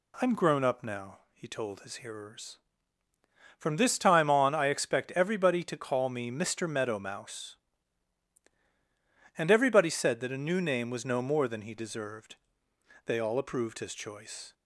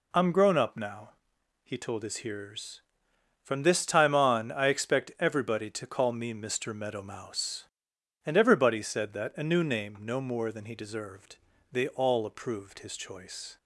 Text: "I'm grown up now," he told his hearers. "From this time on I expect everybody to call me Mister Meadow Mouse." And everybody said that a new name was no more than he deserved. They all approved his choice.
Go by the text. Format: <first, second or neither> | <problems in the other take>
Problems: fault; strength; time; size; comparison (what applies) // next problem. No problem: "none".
first | skips "was"; at 9.9 s